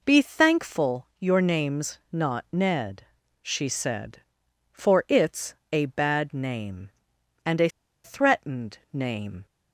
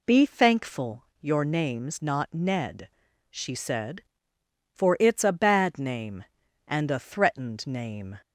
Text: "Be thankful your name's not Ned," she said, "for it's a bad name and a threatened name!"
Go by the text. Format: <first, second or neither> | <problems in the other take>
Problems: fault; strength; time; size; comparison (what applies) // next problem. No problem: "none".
second | pauses between "it's" and "a"; slight; at 5.5 s; 0.16 s long // pauses between "a" and "threatened"; slight; at 7.6 s; 0.36 s long